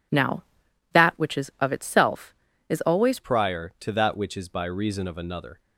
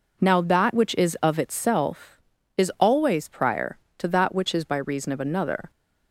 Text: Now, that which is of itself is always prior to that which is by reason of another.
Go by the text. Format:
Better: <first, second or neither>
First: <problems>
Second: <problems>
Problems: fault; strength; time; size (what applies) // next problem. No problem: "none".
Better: second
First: changes voice at "prior"; from 3.2 s on; 2.3 s long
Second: none